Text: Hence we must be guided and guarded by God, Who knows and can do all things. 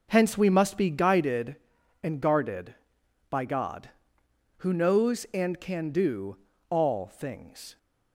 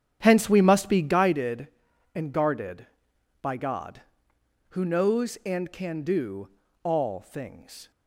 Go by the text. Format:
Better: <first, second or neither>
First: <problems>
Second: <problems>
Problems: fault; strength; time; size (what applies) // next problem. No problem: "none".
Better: first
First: pauses between "do" and "all"; slight; at 6.3 s; 0.34 s long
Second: starts louder than the rest; strong; until 1.4 s; 9 dB // pauses between "do" and "all"; slight; at 6.4 s; 0.36 s long